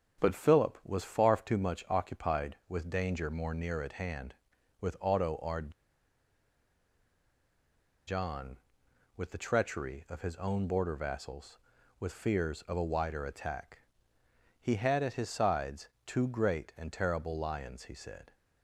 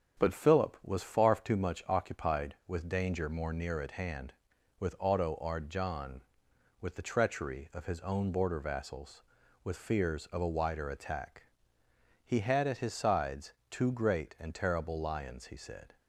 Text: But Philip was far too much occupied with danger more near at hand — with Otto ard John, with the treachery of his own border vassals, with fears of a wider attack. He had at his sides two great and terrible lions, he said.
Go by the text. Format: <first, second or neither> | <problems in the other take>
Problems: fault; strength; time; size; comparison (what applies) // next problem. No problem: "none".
second | starts louder than the rest; strong; until 1.2 s; 7.5 dB; strong in the second // pauses between "ard" and "John"; strong; at 5.7 s; 2.3 s long // pauses between "sides" and "two"; slight; at 15.8 s; 0.18 s long; slight in the second